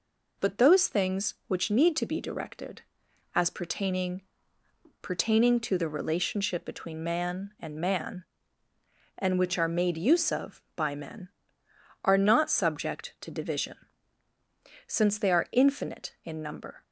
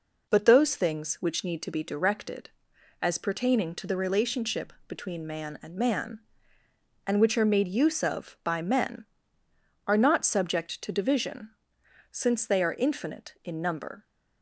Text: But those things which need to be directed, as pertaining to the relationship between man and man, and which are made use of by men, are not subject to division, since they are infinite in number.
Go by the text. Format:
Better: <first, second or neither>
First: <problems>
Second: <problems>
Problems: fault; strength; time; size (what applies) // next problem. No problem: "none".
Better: second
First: says "pertaining" twice; at 5.0 s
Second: none